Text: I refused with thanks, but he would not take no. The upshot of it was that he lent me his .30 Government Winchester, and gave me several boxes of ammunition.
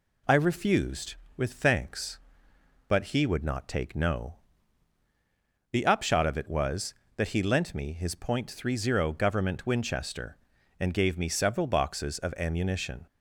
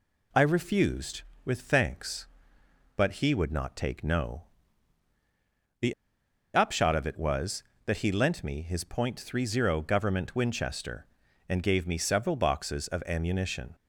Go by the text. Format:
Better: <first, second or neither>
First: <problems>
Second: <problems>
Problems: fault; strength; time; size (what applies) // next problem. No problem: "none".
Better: first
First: none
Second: pauses between "The" and "upshot"; noticeable; at 5.9 s; 0.61 s long